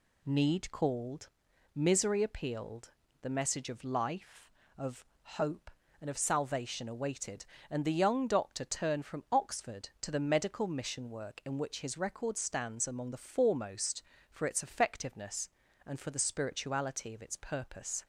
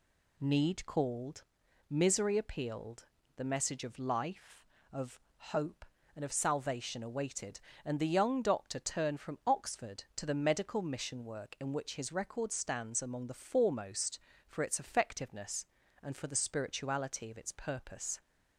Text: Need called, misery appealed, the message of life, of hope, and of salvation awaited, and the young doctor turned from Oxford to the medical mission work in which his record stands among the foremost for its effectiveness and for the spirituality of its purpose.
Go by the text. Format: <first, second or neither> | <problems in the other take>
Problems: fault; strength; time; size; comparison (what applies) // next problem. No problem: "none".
neither | pauses between "of" and "hope"; slight; the same in both